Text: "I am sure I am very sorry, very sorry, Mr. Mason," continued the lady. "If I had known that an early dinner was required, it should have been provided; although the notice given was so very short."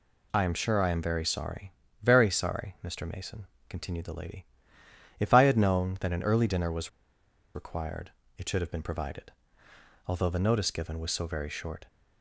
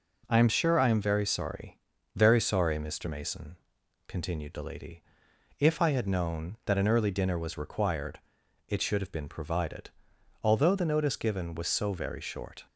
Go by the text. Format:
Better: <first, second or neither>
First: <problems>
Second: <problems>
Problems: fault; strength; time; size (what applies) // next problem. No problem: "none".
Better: second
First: pauses between "was" and "required"; noticeable; at 6.8 s; 0.64 s long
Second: none